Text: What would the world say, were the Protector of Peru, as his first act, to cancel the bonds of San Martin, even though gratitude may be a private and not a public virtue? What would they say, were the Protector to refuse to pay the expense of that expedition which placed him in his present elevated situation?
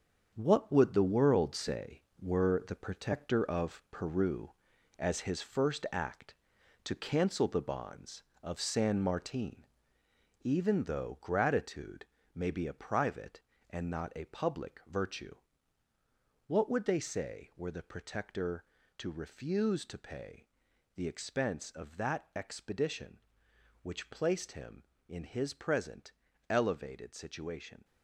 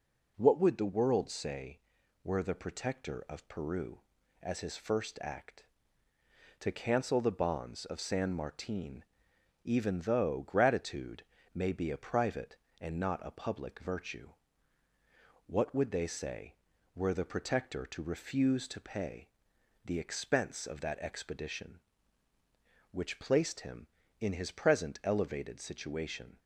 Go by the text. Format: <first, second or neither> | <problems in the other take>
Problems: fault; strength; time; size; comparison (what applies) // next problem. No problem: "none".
second | gets quieter; strong; throughout; 8.5 dB // pauses between "gratitude" and "may"; slight; at 12.0 s; 0.28 s long; slight in the second // pauses between "pay" and "the"; noticeable; at 20.4 s; 0.48 s long; noticeable in the second // pauses between "present" and "elevated"; slight; at 26.1 s; 0.36 s long